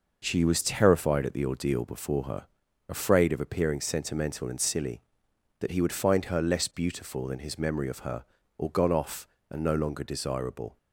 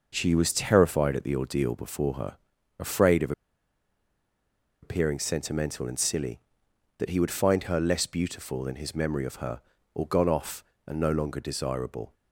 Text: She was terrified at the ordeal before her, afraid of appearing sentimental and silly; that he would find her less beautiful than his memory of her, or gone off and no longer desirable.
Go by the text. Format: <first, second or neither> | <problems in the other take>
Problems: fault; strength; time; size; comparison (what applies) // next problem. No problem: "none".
first | pauses between "of" and "appearing"; strong; at 3.3 s; 1.5 s long